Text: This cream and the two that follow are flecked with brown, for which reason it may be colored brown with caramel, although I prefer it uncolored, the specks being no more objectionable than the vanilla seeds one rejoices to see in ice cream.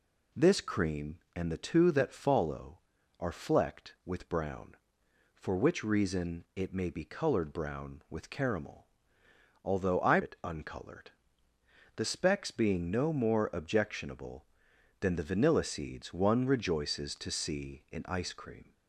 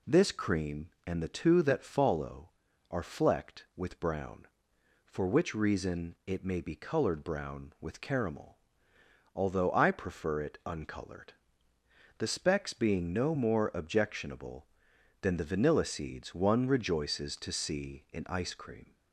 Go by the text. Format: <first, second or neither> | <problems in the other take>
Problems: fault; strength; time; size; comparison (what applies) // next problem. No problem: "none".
second | skips "prefer"; at 10.2 s